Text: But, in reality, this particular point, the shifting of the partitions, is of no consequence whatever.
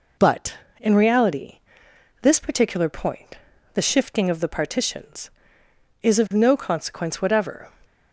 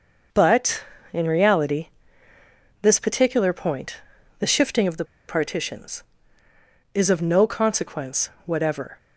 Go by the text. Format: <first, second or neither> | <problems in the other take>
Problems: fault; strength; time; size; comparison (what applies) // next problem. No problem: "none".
first | pauses between "the" and "partitions"; slight; at 5.0 s; 0.23 s long // pauses between "consequence" and "whatever"; slight; at 8.2 s; 0.16 s long